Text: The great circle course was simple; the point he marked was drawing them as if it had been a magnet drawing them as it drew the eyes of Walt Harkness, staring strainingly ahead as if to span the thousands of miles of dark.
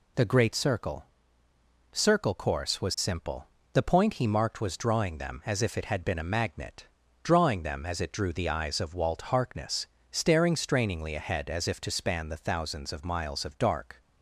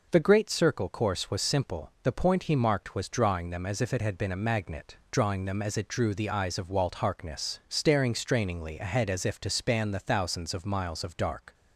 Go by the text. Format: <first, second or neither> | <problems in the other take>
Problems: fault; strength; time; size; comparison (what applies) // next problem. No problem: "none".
second | says "circle" twice; at 1.9 s // pauses between "magnet" and "drawing"; slight; at 6.8 s; 0.34 s long; slight in the second